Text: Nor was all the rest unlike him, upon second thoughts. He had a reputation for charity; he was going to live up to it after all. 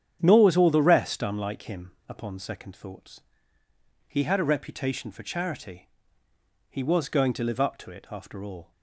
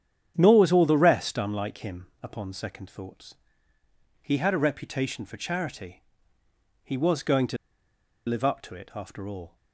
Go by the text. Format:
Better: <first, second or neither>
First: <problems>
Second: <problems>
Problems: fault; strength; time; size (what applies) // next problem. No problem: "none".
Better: first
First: starts louder than the rest; strong; until 1.2 s; 9 dB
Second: starts louder than the rest; strong; until 1.3 s; 9 dB // pauses between "to" and "live"; noticeable; at 7.5 s; 0.70 s long